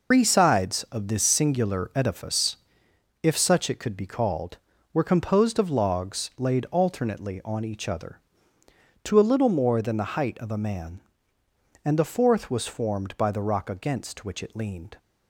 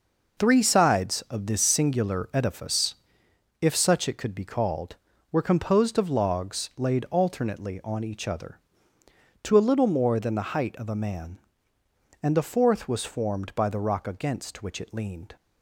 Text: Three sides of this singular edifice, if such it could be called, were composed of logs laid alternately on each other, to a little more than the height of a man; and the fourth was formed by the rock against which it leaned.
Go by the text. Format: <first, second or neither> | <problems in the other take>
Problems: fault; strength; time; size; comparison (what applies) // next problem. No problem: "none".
second | loses the start of "Three"; at 0.1 s; 100 ms